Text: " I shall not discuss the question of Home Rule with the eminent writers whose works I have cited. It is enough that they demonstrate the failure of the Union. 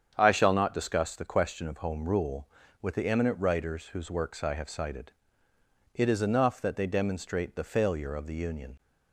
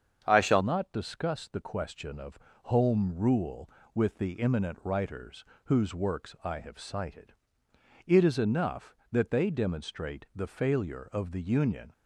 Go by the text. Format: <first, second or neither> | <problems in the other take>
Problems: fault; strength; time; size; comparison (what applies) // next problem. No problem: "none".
first | starts louder than the rest; strong; until 1.2 s; 7.5 dB; strong in the first // changes voice at "not"; from 0.6 s on; 11.3 s long // pauses between "of" and "Home"; slight; at 2.4 s; 0.24 s long // pauses between "writers" and "whose"; slight; at 5.4 s; 0.22 s long